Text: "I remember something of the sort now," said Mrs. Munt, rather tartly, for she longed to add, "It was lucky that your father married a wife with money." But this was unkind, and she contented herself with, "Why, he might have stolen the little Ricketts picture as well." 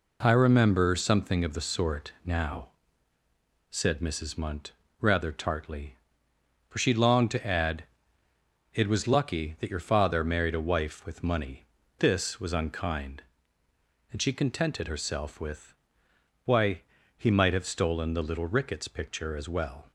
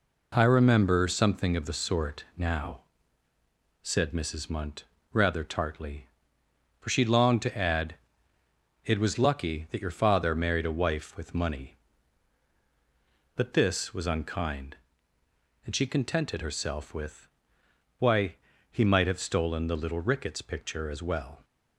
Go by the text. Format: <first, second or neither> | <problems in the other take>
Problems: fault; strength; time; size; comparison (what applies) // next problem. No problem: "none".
second | skips "But"; at 11.8 s